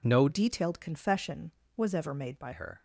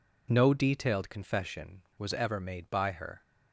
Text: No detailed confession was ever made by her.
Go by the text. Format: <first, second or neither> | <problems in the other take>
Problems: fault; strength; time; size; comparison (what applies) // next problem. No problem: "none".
second | changes voice from "detailed" to "by"; from 0.2 to 2.5 s; 2.3 s long